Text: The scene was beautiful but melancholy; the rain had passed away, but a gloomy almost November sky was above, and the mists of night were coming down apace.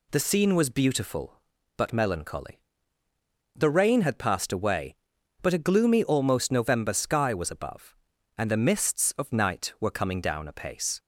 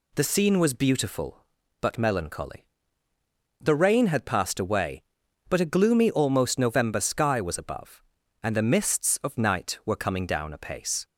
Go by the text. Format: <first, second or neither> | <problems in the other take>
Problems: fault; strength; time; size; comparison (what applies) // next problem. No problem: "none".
neither | none